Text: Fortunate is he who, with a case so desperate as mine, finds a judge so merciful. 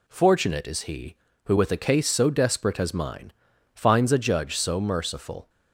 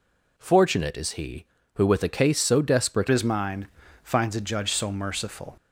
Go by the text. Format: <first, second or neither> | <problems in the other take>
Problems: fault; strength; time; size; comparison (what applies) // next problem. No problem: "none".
first | changes voice at "as"; from 3.0 s on; 2.5 s long